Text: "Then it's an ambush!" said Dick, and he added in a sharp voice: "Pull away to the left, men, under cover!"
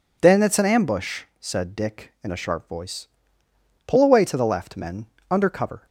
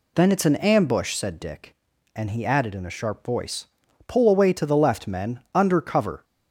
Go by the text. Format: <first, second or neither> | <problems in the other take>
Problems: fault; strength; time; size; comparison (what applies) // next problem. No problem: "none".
second | skips "and he added"; at 2.1 s